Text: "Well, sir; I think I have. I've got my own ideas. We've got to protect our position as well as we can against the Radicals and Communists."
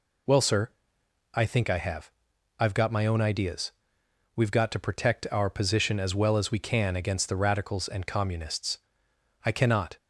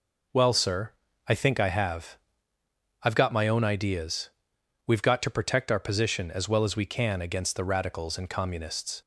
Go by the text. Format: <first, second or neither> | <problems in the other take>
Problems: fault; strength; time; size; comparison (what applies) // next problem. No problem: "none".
second | goes on to say "I cannot"; from 9.4 s on; 0.50 s long